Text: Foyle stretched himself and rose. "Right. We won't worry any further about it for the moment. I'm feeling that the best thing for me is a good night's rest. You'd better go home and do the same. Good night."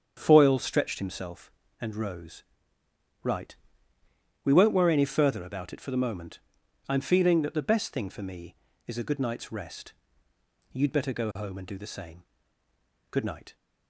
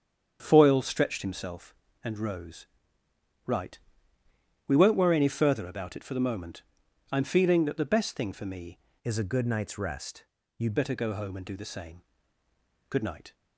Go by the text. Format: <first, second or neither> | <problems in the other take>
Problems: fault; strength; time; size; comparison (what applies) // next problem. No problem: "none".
first | starts louder than the rest; strong; until 1.4 s; 7.5 dB; strong in the first // changes voice from "is" to "You'd"; from 9.0 to 10.7 s; 1.7 s long